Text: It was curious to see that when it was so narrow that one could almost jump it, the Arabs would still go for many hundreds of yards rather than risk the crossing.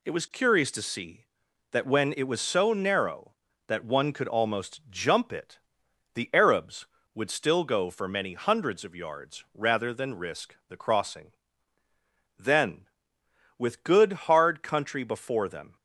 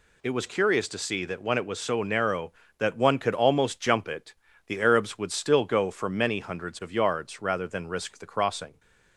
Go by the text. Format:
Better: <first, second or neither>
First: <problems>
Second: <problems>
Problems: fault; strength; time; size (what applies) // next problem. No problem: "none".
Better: second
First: goes on to say "Then with good hard country before them"; strong; from 12.3 s on; 3.3 s long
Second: none